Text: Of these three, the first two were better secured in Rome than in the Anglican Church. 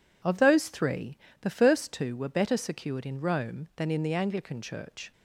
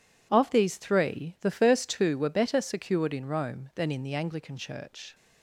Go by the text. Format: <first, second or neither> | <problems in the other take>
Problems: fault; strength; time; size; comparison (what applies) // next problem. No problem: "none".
second | says "those" for "these"; at 0.3 s